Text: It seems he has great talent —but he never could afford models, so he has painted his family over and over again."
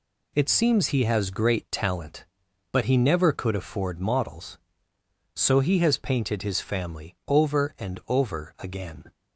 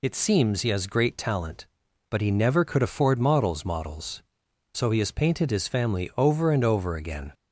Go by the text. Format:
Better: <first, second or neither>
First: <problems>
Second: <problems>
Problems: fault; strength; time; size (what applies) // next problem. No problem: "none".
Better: first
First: none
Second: says "models" twice; at 3.6 s